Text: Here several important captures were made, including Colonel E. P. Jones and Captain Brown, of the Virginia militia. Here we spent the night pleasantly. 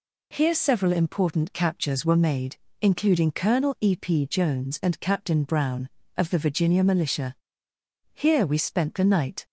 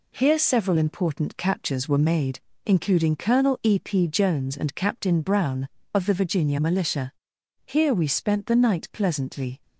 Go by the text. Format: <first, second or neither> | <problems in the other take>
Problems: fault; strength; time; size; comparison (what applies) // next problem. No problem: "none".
second | stops before "pleasantly"; at 9.4 s